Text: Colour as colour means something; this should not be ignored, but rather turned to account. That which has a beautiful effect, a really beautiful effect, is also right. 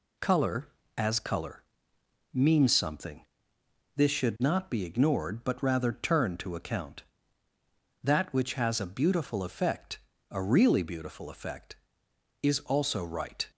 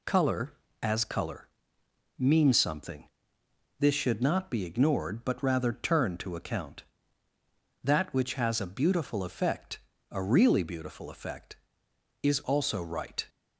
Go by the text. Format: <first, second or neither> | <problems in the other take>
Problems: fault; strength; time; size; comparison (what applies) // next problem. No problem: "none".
neither | pauses between "colour" and "means"; noticeable; the same in both